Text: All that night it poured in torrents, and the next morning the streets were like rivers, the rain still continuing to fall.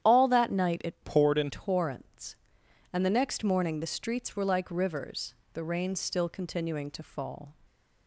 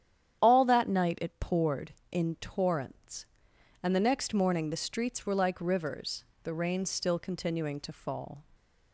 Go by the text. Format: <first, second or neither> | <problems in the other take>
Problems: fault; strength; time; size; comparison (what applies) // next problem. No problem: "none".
second | starts louder than the rest; strong; until 1.1 s; 10 dB; strong in the second // changes voice from "poured" to "in"; from 1.0 to 1.4 s; 0.4 s long